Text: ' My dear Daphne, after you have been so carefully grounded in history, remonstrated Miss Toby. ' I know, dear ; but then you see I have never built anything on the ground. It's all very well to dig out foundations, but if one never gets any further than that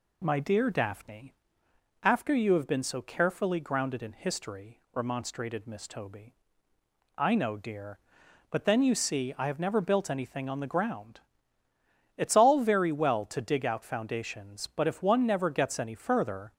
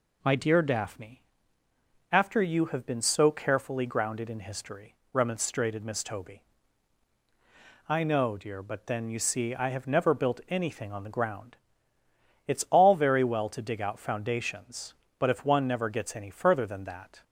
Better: second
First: stops before "than that"; at 16.5 s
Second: none

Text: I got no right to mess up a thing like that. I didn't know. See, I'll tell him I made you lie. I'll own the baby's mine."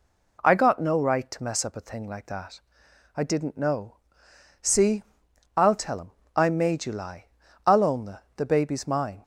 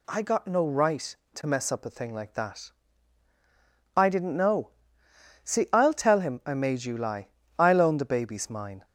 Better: second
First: pauses between "him" and "I"; slight; at 6.1 s; 0.26 s long // says "the" twice; at 8.3 s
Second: none

